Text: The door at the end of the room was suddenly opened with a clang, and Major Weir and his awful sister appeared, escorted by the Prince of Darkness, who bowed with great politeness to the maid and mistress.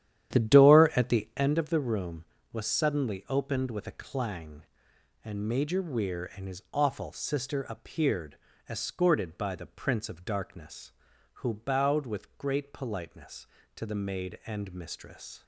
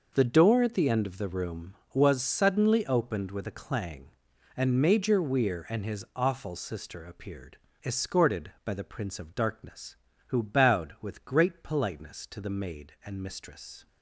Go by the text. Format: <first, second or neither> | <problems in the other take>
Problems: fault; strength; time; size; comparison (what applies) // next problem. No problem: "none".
second | starts louder than the rest; strong; until 1.6 s; 11 dB